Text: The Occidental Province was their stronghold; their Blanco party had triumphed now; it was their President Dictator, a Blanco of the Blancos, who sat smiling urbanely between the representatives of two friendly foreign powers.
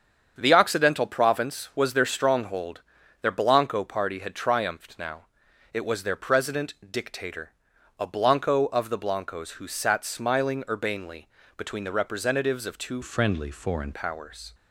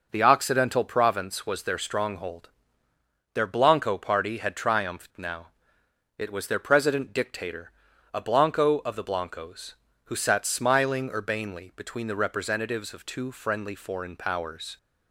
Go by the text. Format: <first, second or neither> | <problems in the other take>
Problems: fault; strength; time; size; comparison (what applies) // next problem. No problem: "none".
second | starts louder than the rest; strong; until 1.3 s; 7.5 dB // pauses between "President" and "Dictator"; slight; at 6.7 s; 0.16 s long // pauses between "urbanely" and "between"; slight; at 11.2 s; 0.28 s long // changes voice from "friendly" to "foreign"; from 13.0 to 13.9 s; 0.9 s long